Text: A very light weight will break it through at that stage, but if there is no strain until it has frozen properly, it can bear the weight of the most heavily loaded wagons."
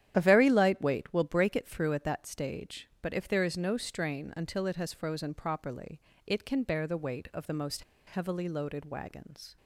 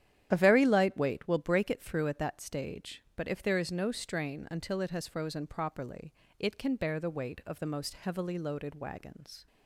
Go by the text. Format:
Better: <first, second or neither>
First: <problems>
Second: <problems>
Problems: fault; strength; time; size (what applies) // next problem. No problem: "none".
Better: second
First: starts louder than the rest; strong; until 1.1 s; 10 dB // pauses between "most" and "heavily"; slight; at 7.8 s; 0.25 s long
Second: starts louder than the rest; strong; until 1.3 s; 10.5 dB